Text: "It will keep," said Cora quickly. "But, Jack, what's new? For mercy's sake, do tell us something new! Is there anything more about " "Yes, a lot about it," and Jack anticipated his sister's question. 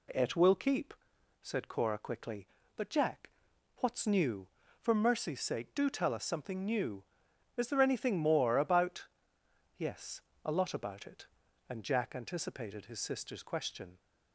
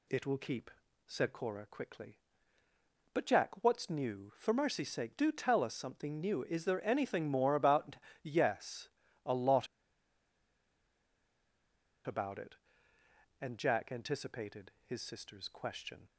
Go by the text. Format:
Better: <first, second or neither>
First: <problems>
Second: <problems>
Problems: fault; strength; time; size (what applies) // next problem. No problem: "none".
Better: first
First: none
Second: pauses between "lot" and "about"; strong; at 9.6 s; 2.3 s long